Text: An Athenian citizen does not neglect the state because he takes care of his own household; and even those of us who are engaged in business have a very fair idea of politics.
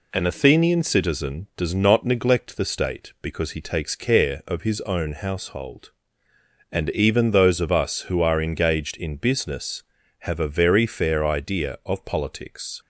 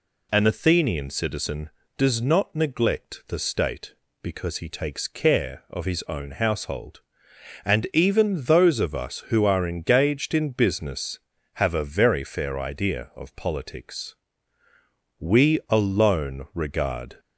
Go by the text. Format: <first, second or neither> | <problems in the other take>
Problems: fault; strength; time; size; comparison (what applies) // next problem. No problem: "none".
first | goes on to say "We alone regard"; strong; from 15.1 s on; 2.0 s long